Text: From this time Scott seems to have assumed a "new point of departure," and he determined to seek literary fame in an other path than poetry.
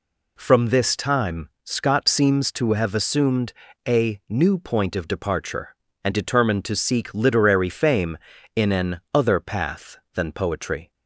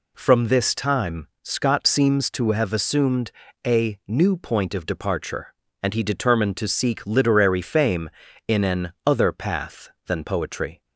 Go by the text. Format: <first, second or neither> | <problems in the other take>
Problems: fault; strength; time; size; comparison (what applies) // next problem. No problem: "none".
second | pauses between "time" and "Scott"; slight; at 1.4 s; 0.16 s long; slight in the second // pauses between "assumed" and "a"; slight; at 3.5 s; 0.34 s long; slight in the second // skips "he"; at 6.1 s